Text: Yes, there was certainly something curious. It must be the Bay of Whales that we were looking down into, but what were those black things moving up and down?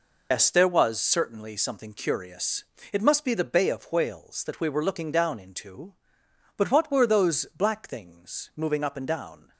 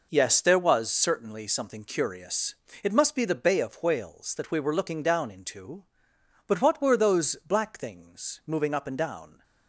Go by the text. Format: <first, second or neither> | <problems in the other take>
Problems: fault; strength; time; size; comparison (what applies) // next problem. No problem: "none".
second | loses the start of "Yes"; at 0.3 s; 115 ms